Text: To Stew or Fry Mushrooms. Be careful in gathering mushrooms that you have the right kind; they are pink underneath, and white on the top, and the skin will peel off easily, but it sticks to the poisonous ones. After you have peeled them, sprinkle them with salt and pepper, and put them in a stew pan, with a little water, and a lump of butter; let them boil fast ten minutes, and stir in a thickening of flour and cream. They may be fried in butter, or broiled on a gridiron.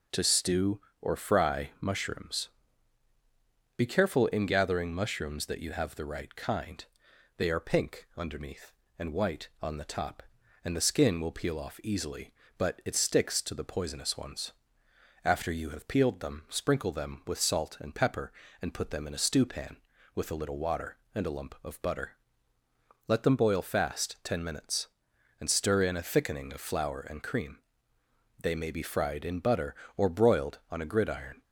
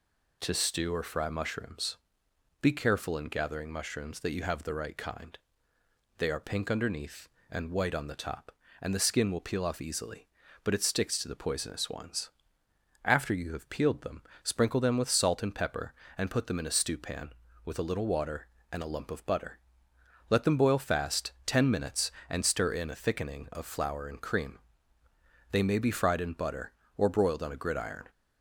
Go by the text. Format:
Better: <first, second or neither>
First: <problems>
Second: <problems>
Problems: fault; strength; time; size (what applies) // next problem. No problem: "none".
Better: neither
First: none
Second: none